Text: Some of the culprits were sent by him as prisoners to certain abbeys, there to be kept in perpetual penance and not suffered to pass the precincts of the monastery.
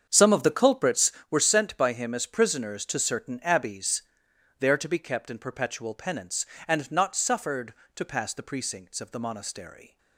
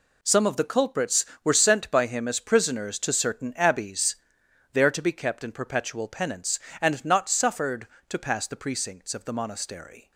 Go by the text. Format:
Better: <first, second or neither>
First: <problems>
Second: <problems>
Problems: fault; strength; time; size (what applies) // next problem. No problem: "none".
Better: second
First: starts louder than the rest; strong; until 1.2 s; 7.5 dB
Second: none